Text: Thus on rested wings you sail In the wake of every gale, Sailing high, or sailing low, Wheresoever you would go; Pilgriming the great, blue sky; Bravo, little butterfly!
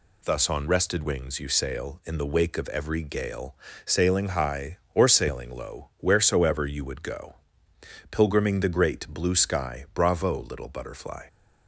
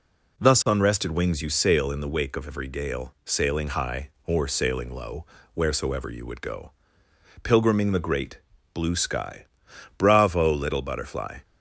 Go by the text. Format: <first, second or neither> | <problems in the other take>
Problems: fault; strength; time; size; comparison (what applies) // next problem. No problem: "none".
neither | none